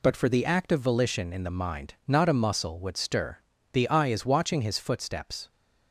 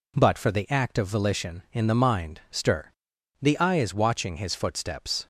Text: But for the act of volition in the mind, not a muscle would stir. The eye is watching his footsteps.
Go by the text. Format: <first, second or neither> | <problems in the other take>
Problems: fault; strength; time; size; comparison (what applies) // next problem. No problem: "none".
first | skips "not a muscle would"; at 2.4 s